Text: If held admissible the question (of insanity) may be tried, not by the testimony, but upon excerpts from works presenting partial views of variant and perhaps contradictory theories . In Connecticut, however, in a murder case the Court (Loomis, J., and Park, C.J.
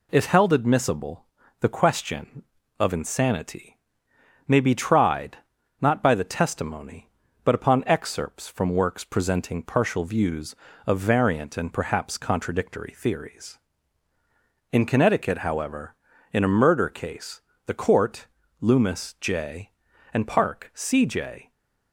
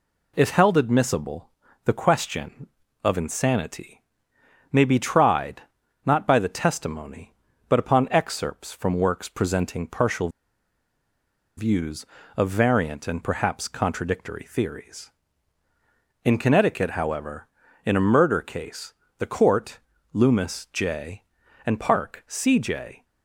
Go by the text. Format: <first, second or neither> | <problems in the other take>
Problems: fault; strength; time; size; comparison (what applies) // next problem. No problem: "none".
first | pauses between "admissible" and "the"; slight; at 1.5 s; 0.34 s long; slight in the first // pauses between "partial" and "views"; strong; at 10.2 s; 1.2 s long // pauses between "case" and "the"; slight; at 18.9 s; 0.24 s long; slight in the first